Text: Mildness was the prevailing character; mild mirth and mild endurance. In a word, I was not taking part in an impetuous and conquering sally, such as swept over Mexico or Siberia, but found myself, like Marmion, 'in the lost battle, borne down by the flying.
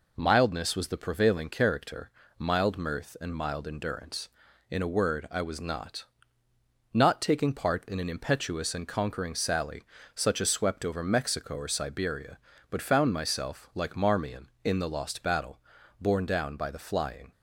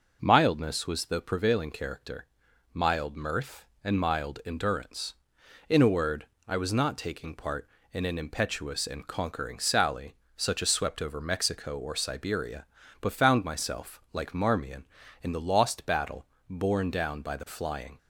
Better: second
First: says "not" twice; at 6.9 s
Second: none

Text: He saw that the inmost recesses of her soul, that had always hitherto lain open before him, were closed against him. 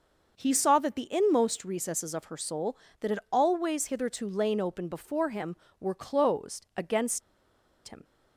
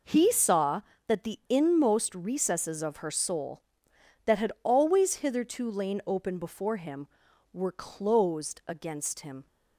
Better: second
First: starts louder than the rest; noticeable; until 1.3 s; 6 dB // pauses between "against" and "him"; noticeable; at 7.2 s; 0.66 s long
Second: none

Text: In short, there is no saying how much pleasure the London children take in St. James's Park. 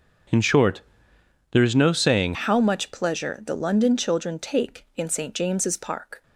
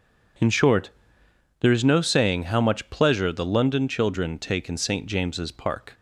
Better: second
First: starts louder than the rest; until 2.0 s; 6.5 dB // changes voice at "how"; from 2.3 s on; 3.9 s long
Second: none

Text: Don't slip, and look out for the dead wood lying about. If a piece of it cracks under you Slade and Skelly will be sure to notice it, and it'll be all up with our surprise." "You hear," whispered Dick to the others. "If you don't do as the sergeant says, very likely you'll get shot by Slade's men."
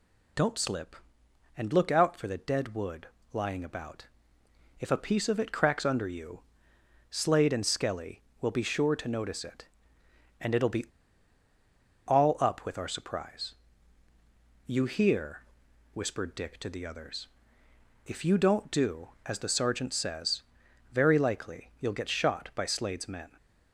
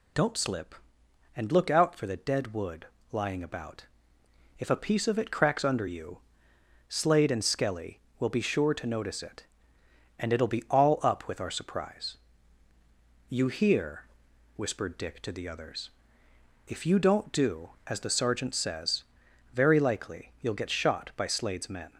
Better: second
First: pauses between "wood" and "lying"; slight; at 3.0 s; 0.26 s long // pauses between "you" and "Slade"; noticeable; at 6.4 s; 0.70 s long // pauses between "be" and "all"; at 10.8 s; 1.2 s long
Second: pauses between "wood" and "lying"; slight; at 2.8 s; 0.26 s long // pauses between "you" and "Slade"; noticeable; at 6.1 s; 0.70 s long

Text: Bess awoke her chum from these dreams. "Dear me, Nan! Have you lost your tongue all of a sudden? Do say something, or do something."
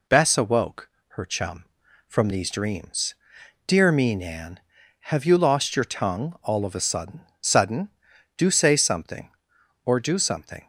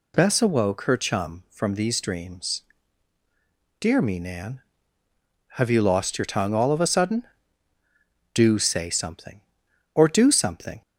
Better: second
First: pauses between "awoke" and "her"; slight; at 0.8 s; 0.20 s long // says "sudden" twice; at 7.4 s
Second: none

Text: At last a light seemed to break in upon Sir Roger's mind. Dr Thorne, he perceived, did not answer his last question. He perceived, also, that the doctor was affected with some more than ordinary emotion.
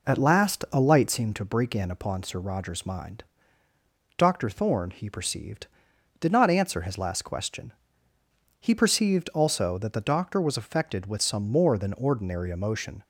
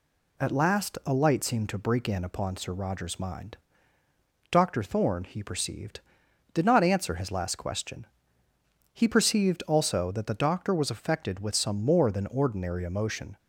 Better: second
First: starts louder than the rest; noticeable; until 1.2 s; 4.5 dB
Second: none

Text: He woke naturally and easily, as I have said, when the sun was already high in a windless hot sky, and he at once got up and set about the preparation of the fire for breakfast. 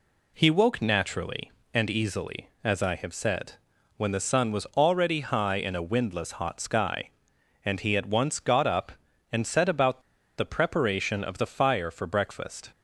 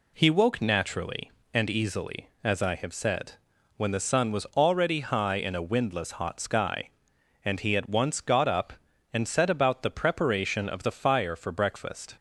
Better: second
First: pauses between "about" and "the"; at 10.0 s; 0.36 s long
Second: none

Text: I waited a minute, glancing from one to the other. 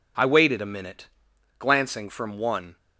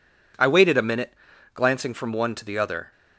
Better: second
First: stops before "to the other"; at 2.7 s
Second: none

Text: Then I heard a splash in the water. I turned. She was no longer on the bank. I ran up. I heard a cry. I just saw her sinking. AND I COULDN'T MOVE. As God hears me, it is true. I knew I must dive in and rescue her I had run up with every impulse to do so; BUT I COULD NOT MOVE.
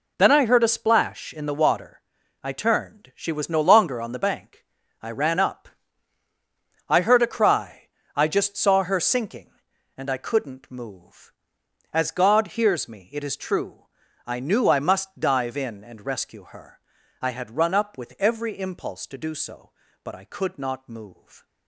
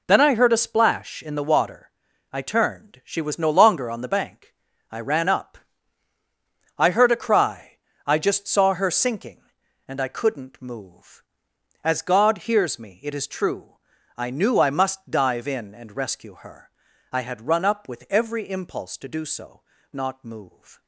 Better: first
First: pauses between "her" and "I"; at 16.7 s; 0.42 s long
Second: pauses between "her" and "I"; at 16.6 s; 0.42 s long // skips "BUT I COULD"; at 19.7 s

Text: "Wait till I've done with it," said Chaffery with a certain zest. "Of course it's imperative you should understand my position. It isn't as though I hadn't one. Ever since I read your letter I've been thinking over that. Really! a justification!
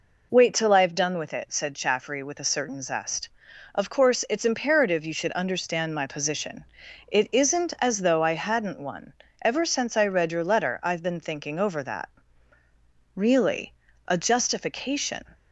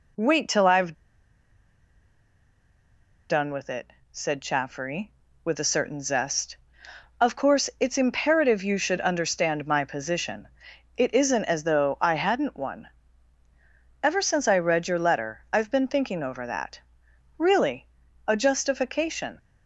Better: first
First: none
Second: pauses between "I've" and "done"; strong; at 0.9 s; 2.3 s long

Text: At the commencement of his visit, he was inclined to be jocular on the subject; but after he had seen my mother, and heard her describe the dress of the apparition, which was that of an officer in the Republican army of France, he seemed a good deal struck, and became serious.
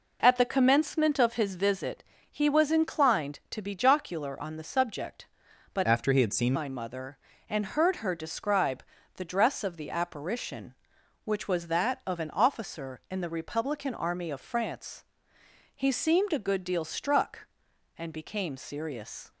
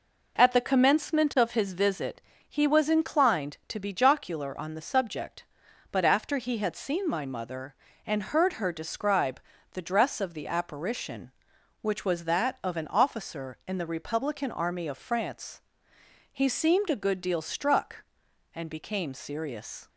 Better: second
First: changes voice from "after" to "seen"; from 5.8 to 6.5 s; 0.7 s long // pauses between "describe" and "the"; slight; at 8.8 s; 0.32 s long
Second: pauses between "describe" and "the"; slight; at 9.4 s; 0.32 s long

